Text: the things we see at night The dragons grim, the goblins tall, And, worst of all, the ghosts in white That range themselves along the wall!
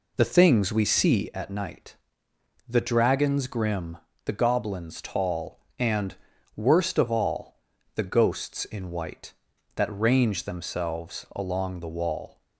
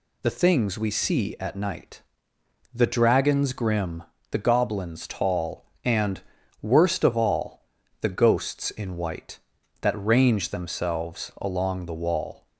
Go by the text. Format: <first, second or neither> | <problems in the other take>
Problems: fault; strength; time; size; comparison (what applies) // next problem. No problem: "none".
second | starts louder than the rest; slight; until 1.3 s; 3.5 dB // pauses between "night" and "The"; noticeable; at 1.9 s; 0.72 s long; noticeable in the second